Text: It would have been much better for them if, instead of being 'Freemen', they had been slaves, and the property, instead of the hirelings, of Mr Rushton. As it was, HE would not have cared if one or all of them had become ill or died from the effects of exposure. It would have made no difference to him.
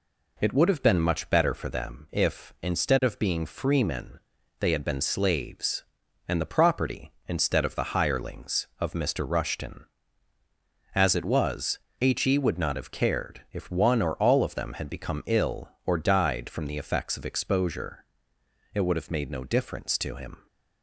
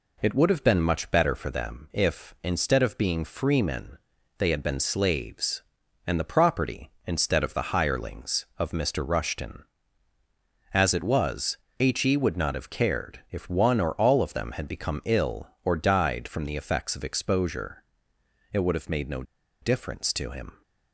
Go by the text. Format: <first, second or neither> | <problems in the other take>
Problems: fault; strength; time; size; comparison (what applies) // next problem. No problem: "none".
first | pauses between "no" and "difference"; at 19.2 s; 0.39 s long